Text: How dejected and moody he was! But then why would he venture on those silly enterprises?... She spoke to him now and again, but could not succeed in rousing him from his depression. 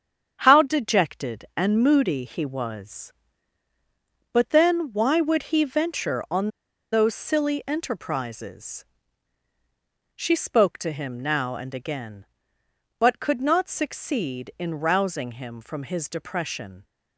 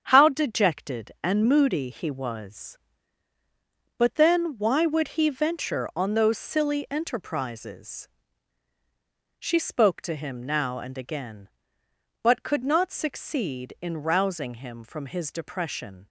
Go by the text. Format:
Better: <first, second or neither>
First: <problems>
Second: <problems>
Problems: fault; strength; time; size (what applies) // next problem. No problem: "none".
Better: second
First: starts louder than the rest; strong; until 1.4 s; 7.5 dB // pauses between "on" and "those"; at 6.4 s; 0.42 s long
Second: starts louder than the rest; strong; until 1.0 s; 7.5 dB